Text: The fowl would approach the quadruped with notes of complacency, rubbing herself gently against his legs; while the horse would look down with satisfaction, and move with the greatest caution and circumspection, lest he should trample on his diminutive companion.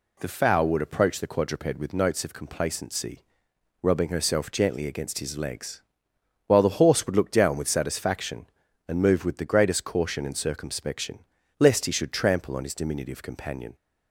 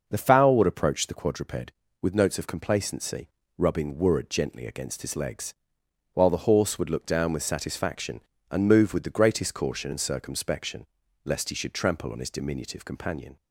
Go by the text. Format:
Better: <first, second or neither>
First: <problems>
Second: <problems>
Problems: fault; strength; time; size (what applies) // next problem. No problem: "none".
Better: first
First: none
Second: says "wurrud" for "herself"; at 3.9 s